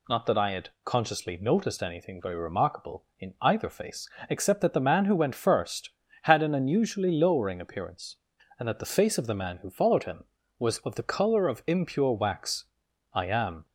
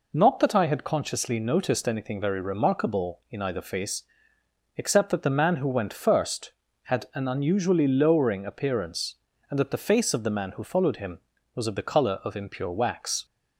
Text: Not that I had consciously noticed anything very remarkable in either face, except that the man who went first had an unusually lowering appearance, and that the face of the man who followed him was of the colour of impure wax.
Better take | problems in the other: second | goes on to say "I am"; from 13.1 s on; 0.52 s long

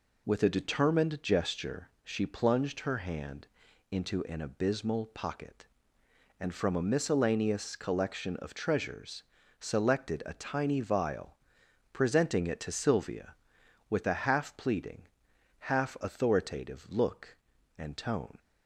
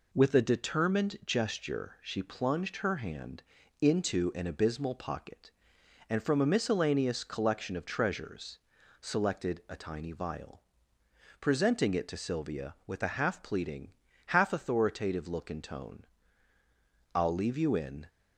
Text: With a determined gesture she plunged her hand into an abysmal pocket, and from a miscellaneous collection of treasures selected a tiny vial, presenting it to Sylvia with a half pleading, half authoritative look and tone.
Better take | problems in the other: first | pauses between "hand" and "into"; slight; at 3.4 s; 0.36 s long; also in the first // pauses between "treasures" and "selected"; at 8.5 s; 0.42 s long; also in the first // goes on to say "I'll leave you in"; noticeable; from 17.1 s on; 0.94 s long

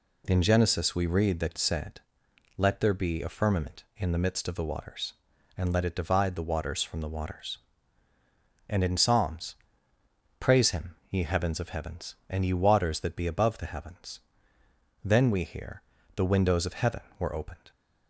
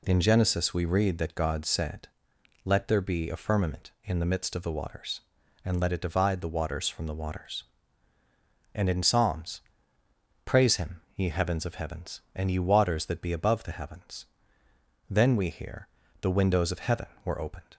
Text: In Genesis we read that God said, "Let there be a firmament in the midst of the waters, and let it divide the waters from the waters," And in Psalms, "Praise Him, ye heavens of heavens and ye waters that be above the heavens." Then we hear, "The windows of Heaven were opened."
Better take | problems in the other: second | skips "God"; at 1.5 s

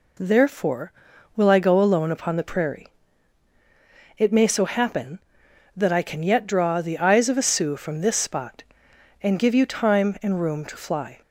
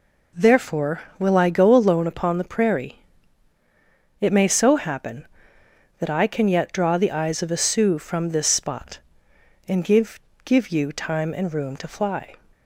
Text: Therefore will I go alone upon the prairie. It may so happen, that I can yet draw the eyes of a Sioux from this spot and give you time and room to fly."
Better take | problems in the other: first | says "give" twice; at 10.4 s

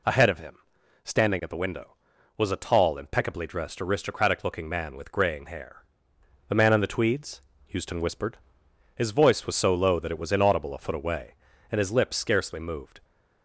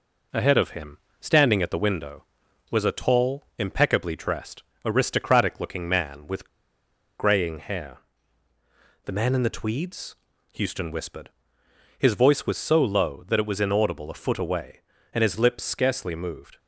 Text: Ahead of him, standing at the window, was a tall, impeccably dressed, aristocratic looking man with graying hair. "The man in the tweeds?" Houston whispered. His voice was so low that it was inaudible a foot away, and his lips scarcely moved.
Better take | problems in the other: first | pauses between "with" and "graying"; noticeable; at 6.4 s; 0.70 s long

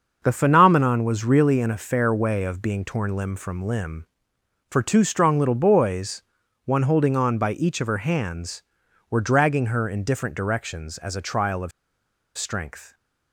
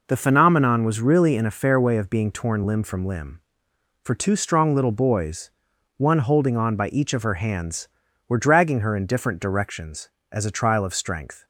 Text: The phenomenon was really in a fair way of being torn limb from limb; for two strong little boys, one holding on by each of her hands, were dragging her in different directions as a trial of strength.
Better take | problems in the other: second | starts louder than the rest; until 1.2 s; 6.5 dB // pauses between "of" and "strength"; noticeable; at 11.7 s; 0.67 s long

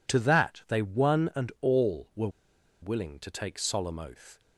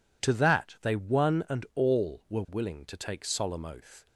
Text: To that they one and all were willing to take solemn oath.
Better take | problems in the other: second | pauses between "were" and "willing"; noticeable; at 2.2 s; 0.52 s long

